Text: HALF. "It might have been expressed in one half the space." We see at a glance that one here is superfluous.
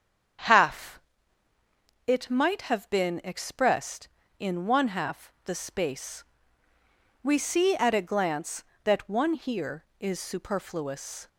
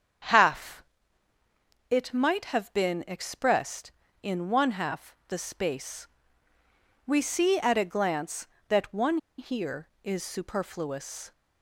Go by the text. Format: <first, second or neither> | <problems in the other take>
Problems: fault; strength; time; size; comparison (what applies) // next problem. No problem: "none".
first | starts louder than the rest; strong; until 2.3 s; 8 dB; strong in the first // pauses between "one" and "here"; slight; at 9.1 s; 0.21 s long